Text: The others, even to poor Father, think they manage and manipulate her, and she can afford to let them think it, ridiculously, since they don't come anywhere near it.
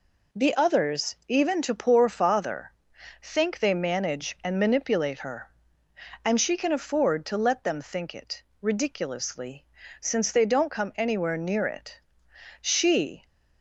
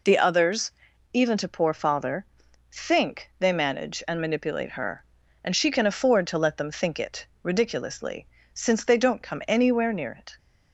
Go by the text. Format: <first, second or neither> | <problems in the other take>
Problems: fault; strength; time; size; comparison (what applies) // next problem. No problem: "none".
second | goes on to say "She"; noticeable; from 12.6 s on; 0.64 s long